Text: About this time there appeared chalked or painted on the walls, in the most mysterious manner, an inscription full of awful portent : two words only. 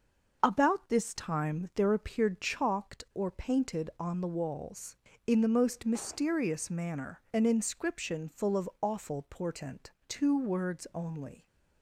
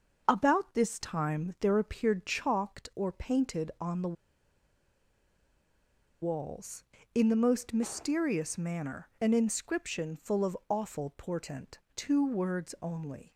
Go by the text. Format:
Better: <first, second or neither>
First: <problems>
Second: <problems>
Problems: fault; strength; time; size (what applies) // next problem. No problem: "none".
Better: first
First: starts louder than the rest; until 1.4 s; 6.5 dB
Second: starts louder than the rest; until 1.2 s; 6.5 dB // pauses between "the" and "walls"; strong; at 4.1 s; 2.0 s long